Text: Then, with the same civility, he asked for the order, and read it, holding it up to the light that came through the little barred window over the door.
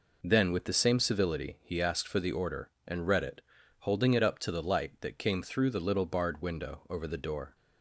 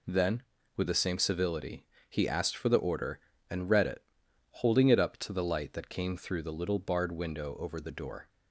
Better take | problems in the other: neither | none

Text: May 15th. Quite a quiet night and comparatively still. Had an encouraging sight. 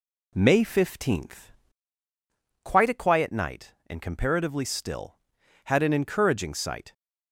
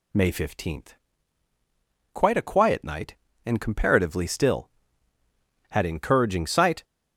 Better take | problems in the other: first | skips "an"; at 5.8 s

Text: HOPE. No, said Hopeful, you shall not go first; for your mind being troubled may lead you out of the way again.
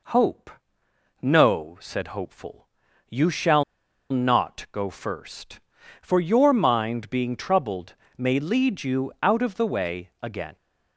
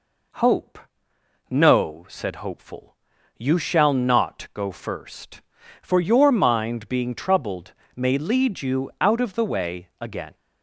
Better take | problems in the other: second | pauses between "shall" and "not"; noticeable; at 3.6 s; 0.48 s long // pauses between "troubled" and "may"; slight; at 7.9 s; 0.20 s long; slight in the second

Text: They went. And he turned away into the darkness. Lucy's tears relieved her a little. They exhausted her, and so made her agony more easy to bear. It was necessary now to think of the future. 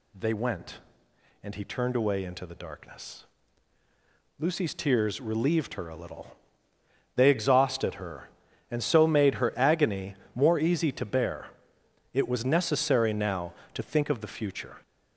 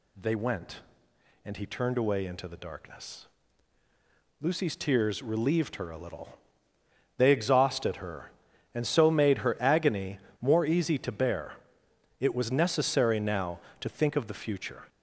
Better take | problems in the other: neither | pauses between "agony" and "more"; slight; the same in both

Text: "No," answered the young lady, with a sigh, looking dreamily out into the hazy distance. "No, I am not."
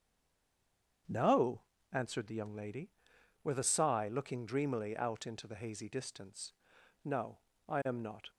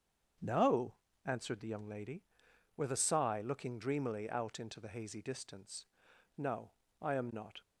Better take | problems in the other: second | stays silent before the first word; until 1.0 s; 1.0 s long // starts louder than the rest; strong; until 2.3 s; 7.5 dB; strong in the second

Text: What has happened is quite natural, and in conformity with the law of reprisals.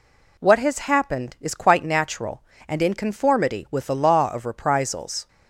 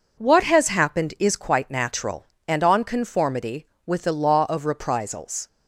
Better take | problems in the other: first | says "on" for "in"; at 2.6 s

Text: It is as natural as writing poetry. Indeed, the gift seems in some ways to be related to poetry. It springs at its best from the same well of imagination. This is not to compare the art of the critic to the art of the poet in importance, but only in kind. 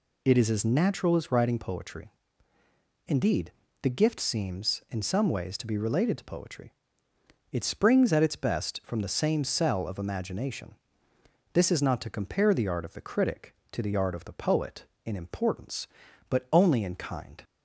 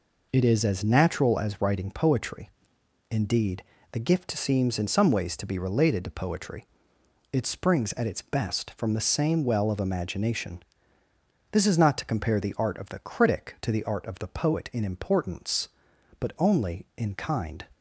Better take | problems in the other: second | says "cell" for "well"; at 9.4 s

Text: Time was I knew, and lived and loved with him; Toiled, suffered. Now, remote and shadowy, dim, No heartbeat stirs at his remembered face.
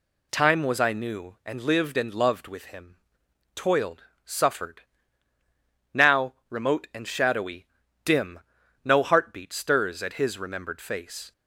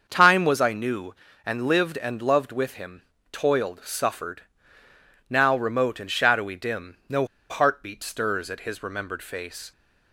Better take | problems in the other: first | starts louder than the rest; until 1.0 s; 6.5 dB // pauses between "No" and "heartbeat"; slight; at 7.2 s; 0.24 s long

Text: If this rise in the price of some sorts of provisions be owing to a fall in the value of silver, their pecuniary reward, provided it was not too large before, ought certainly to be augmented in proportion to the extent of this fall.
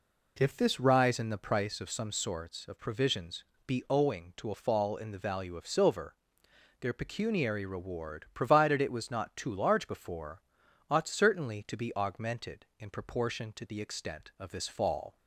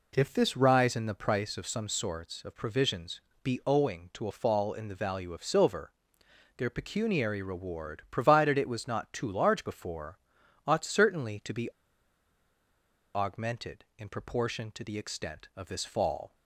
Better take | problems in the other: first | pauses between "provisions" and "be"; slight; at 3.1 s; 0.22 s long; slight in the first // pauses between "be" and "augmented"; strong; at 11.6 s; 1.4 s long

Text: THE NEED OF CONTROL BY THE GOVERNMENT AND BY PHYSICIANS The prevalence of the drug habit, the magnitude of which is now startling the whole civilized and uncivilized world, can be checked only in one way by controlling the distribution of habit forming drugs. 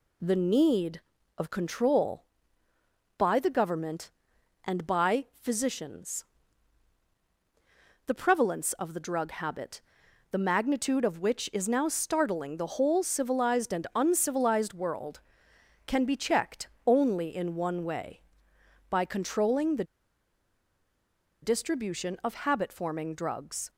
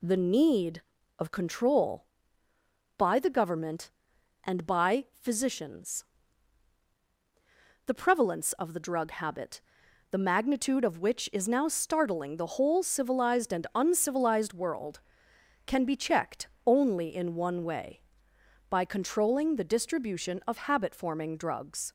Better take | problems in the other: second | pauses between "PHYSICIANS" and "The"; strong; at 6.2 s; 1.8 s long; strong in the second // pauses between "checked" and "only"; slight; at 16.6 s; 0.18 s long; slight in the second // pauses between "the" and "distribution"; strong; at 19.8 s; 1.5 s long

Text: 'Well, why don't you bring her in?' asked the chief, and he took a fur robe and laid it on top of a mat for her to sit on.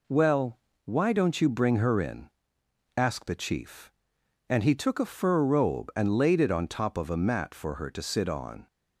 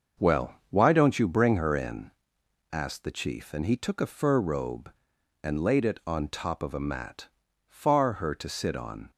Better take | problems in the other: first | starts louder than the rest; until 1.3 s; 6.5 dB // says "far" for "for"; at 7.6 s

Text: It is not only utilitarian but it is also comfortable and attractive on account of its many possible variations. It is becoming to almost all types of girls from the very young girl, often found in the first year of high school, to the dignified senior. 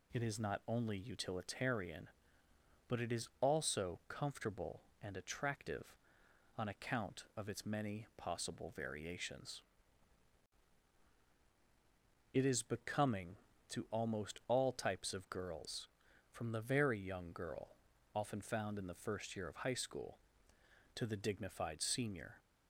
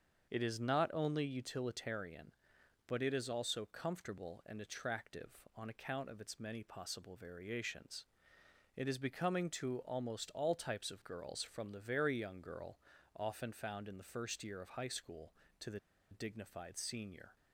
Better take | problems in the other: first | starts louder than the rest; until 1.3 s; 7 dB // pauses between "the" and "dignified"; slight; at 15.7 s; 0.32 s long

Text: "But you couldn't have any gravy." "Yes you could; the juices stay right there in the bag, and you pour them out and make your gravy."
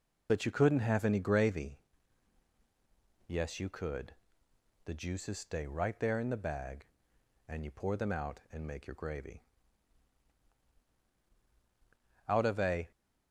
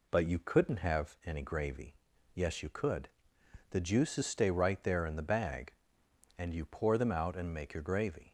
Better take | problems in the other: second | goes on to say "Out of a"; noticeable; from 12.2 s on; 0.62 s long

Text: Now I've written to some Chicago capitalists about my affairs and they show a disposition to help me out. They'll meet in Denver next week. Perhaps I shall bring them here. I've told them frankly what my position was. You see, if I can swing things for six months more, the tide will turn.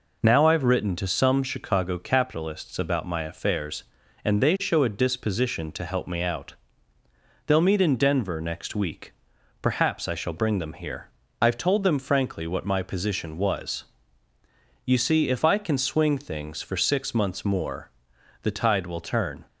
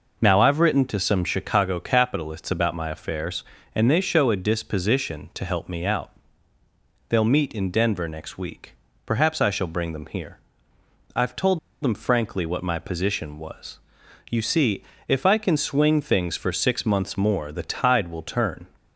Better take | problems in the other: first | pauses between "told" and "them"; slight; at 11.5 s; 0.23 s long

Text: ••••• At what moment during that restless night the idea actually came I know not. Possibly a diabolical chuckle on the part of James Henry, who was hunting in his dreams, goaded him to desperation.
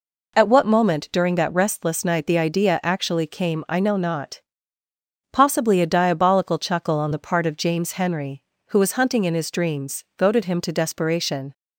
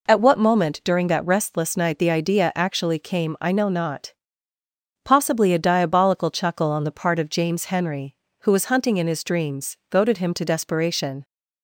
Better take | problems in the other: neither | none

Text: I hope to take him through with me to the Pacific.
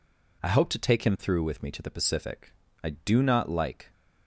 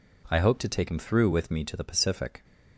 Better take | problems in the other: second | goes on to say "I do not like"; noticeable; from 2.8 s on; 1.1 s long

